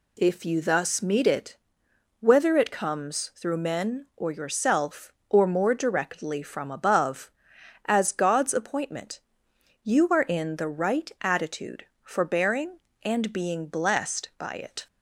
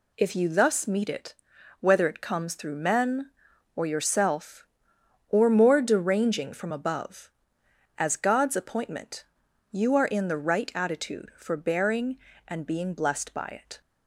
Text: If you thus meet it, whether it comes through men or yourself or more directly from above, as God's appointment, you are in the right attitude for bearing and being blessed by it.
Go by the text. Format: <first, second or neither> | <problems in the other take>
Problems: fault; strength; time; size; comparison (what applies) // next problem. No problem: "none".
first | says "deranging" for "directly"; at 5.8 s